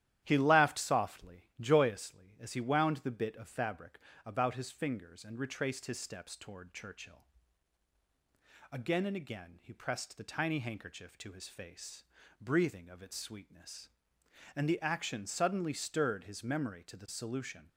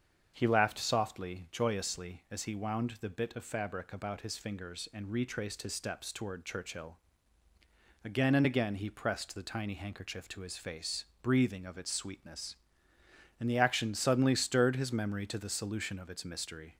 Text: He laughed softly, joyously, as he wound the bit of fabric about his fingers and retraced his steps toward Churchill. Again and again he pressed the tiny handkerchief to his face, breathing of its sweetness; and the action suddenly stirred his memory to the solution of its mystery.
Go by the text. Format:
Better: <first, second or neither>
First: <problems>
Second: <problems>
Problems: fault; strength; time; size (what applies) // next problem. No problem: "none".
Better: second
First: starts louder than the rest; strong; until 1.2 s; 12 dB // pauses between "fabric" and "about"; slight; at 3.9 s; 0.26 s long // stops before "of its mystery"; at 17.6 s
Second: starts louder than the rest; until 1.3 s; 7 dB